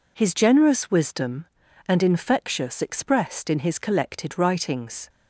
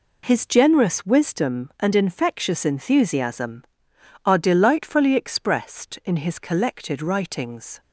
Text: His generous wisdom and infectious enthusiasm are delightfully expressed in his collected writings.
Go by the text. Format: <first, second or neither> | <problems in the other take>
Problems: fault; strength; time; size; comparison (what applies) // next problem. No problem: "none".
second | skips "enthusiasm are delightfully"; at 2.8 s